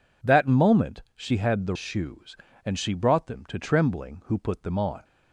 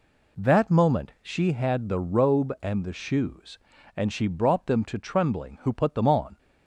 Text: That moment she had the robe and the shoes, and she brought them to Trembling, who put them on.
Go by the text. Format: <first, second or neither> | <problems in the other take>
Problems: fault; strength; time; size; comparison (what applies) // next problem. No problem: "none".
second | skips "robe and the"; at 1.7 s